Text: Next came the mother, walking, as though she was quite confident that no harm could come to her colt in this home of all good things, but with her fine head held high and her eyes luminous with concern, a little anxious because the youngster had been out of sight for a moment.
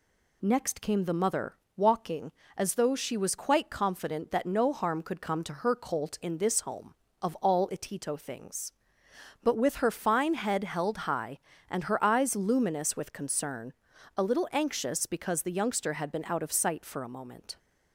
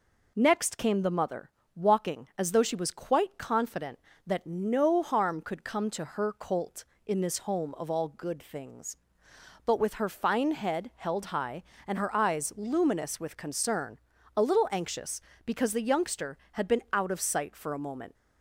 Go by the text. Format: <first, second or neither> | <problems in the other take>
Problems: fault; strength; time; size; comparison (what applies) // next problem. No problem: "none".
second | says "itito" for "good"; at 7.6 s